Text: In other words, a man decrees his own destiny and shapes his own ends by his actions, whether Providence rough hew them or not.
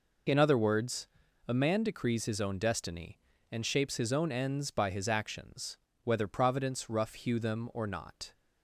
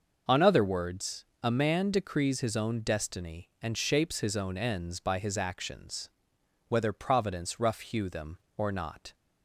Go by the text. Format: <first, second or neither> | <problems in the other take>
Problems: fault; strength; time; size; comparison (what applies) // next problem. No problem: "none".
first | starts louder than the rest; noticeable; until 1.4 s; 6 dB // says "On" for "In"; at 0.2 s